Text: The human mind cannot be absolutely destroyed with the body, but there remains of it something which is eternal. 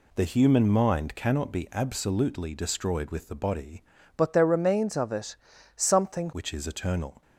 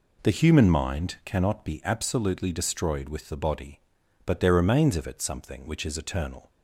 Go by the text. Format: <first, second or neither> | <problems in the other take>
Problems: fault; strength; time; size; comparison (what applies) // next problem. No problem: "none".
second | changes voice from "but" to "something"; from 4.1 to 6.3 s; 2.2 s long // pauses between "it" and "something"; at 5.3 s; 0.40 s long